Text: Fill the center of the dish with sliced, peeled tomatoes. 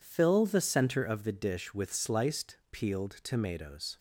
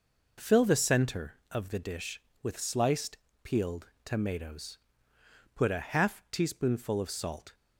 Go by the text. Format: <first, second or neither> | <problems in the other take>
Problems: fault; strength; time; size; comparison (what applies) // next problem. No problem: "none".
first | pauses between "peeled" and "tomatoes"; slight; at 3.8 s; 0.16 s long // goes on to say "Put a half teaspoonful of salt"; strong; from 5.5 s on; 1.9 s long